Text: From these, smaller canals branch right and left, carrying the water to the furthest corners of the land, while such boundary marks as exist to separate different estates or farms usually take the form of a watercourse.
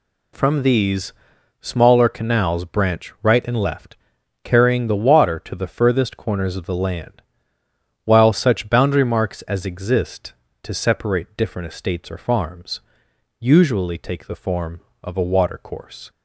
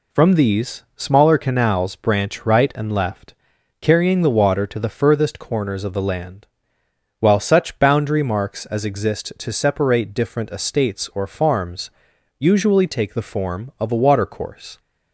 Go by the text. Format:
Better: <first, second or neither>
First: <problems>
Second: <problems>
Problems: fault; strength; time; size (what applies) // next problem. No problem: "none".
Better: neither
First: pauses between "farms" and "usually"; noticeable; at 12.8 s; 0.58 s long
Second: pauses between "farms" and "usually"; noticeable; at 11.8 s; 0.50 s long